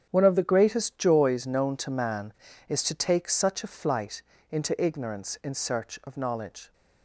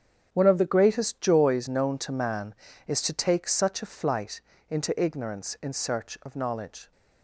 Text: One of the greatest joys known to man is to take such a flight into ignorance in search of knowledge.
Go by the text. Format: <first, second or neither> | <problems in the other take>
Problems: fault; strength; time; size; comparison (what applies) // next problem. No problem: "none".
neither | starts louder than the rest; strong; the same in both // pauses between "flight" and "into"; slight; the same in both